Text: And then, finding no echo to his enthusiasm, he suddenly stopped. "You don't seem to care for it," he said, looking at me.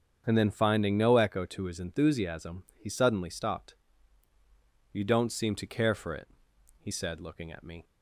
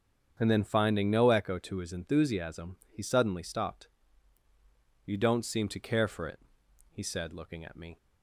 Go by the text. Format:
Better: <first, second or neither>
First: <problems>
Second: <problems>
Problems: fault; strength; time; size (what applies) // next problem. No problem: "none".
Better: neither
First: starts louder than the rest; strong; until 1.2 s; 7 dB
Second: starts louder than the rest; strong; until 1.4 s; 7 dB